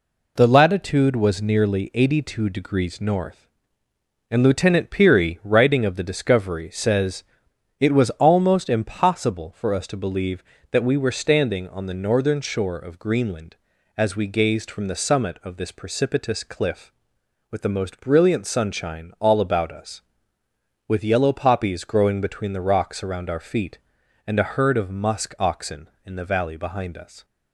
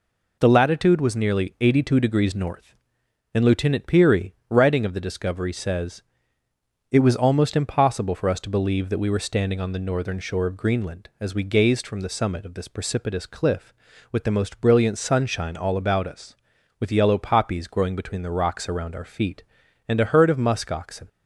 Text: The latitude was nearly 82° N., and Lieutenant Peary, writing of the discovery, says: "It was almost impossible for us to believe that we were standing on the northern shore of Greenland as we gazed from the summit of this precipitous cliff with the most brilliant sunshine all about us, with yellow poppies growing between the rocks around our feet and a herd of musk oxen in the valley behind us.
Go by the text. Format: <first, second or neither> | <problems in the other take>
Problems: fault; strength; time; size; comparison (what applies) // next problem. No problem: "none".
first | stops before "in the valley behind us"; at 21.0 s